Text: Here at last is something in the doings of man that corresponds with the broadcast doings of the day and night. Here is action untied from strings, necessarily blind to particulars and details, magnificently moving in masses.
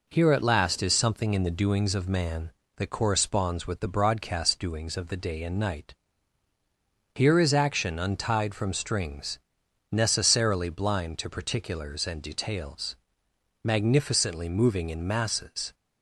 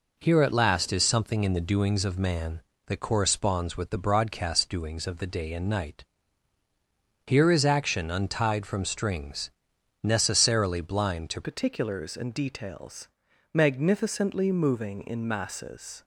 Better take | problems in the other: first | changes voice at "particulars"; from 11.4 s on; 4.6 s long

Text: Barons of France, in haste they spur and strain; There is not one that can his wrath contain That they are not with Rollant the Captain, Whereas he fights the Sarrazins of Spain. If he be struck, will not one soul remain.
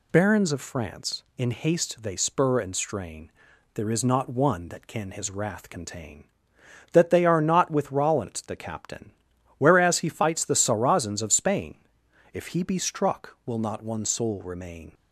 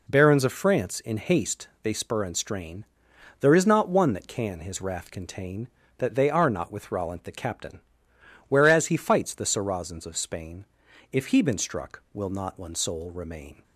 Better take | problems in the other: first | pauses between "haste" and "they"; slight; at 1.6 s; 0.16 s long // says "been" for "be"; at 11.4 s

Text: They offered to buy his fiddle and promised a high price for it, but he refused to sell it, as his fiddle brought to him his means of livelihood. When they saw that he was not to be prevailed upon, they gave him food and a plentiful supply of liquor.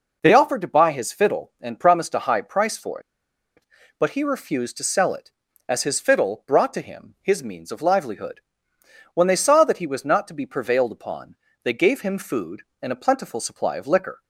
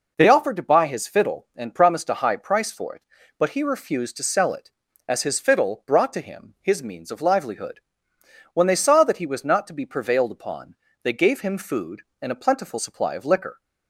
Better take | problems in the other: second | pauses between "for" and "it"; noticeable; at 2.9 s; 0.57 s long

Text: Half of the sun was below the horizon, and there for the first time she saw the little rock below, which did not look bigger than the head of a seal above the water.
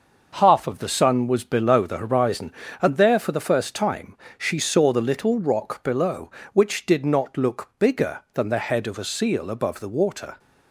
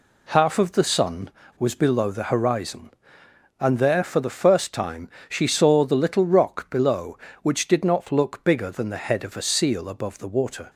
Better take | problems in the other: neither | pauses between "time" and "she"; slight; the same in both

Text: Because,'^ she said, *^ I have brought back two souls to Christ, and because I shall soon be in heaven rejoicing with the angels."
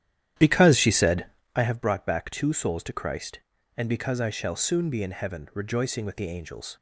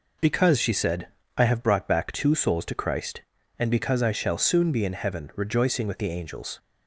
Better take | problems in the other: second | starts louder than the rest; strong; until 1.6 s; 11 dB

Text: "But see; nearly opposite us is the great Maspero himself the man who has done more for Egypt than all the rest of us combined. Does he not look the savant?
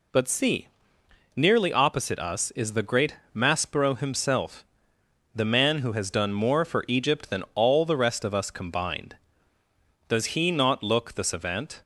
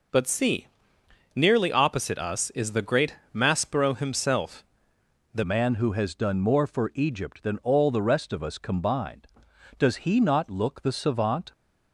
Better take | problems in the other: first | pauses between "great" and "Maspero"; slight; at 3.1 s; 0.18 s long; slight in the first // pauses between "himself" and "the"; noticeable; at 4.6 s; 0.70 s long; noticeable in the first // changes voice at "man"; from 5.4 s on; 6.1 s long

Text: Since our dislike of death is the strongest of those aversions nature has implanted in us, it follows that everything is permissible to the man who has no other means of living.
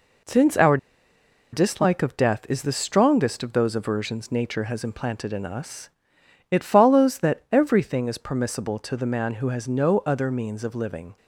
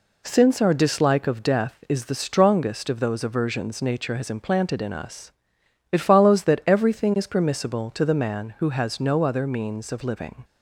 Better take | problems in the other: second | pauses between "our" and "dislike"; noticeable; at 0.7 s; 0.75 s long

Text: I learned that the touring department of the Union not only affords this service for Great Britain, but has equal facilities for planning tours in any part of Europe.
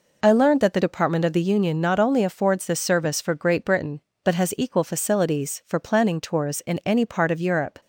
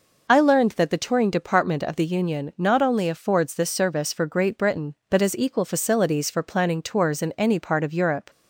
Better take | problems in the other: second | skips "touring"; at 0.8 s

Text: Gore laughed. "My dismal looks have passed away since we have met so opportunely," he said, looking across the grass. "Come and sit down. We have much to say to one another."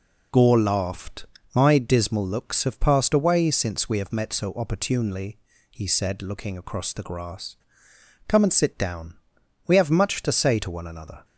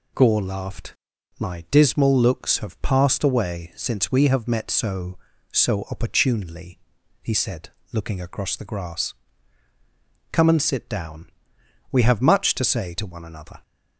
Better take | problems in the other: first | says "so" twice; at 5.5 s

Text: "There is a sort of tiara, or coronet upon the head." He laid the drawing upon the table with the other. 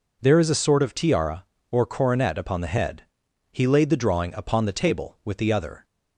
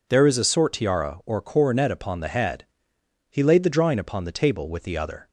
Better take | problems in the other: first | skips "of"; at 0.7 s

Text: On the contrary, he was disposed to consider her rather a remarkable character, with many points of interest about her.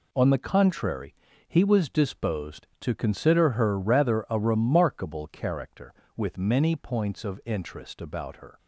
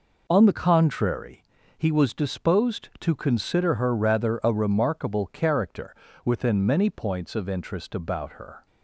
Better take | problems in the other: first | says "within" for "with"; at 6.2 s

